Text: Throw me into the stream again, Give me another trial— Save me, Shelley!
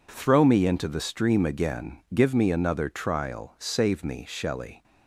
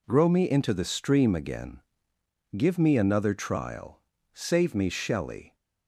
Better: first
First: none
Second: says "Grow" for "Throw"; at 0.0 s

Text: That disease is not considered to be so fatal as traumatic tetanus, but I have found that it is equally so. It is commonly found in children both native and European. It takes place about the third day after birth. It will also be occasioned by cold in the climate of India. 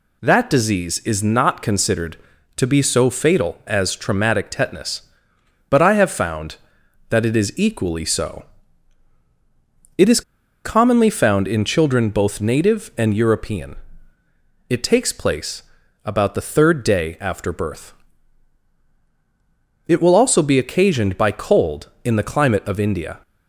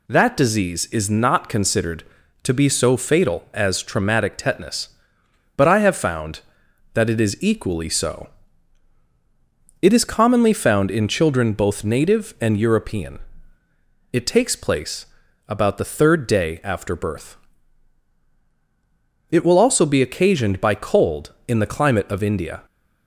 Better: second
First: pauses between "is" and "commonly"; at 10.2 s; 0.43 s long // pauses between "place" and "about"; at 15.6 s; 0.42 s long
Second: pauses between "place" and "about"; at 15.0 s; 0.42 s long

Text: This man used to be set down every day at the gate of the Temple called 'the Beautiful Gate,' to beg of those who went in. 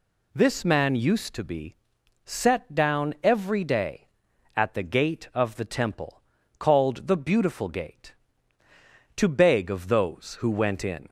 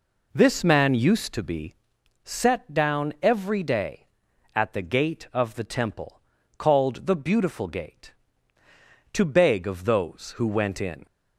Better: first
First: pauses between "be" and "set"; noticeable; at 1.7 s; 0.50 s long // pauses between "Temple" and "called"; at 6.2 s; 0.38 s long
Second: starts louder than the rest; noticeable; until 1.9 s; 4 dB // pauses between "be" and "set"; noticeable; at 1.7 s; 0.50 s long // pauses between "Temple" and "called"; at 6.2 s; 0.38 s long

